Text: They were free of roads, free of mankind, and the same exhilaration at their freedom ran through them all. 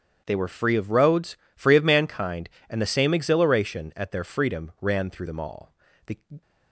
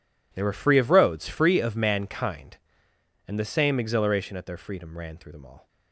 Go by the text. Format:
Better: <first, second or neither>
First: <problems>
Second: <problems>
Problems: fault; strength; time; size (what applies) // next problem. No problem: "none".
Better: second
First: starts louder than the rest; strong; until 1.2 s; 8.5 dB // goes on to say "The"; slight; from 6.0 s on; 0.34 s long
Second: none